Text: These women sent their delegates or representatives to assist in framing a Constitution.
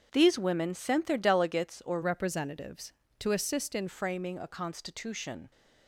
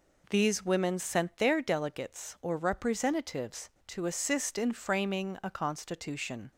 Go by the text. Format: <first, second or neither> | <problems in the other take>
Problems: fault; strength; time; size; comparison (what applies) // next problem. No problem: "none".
second | starts louder than the rest; strong; until 1.1 s; 7.5 dB // changes voice from "representatives" to "in"; from 2.0 to 3.8 s; 1.8 s long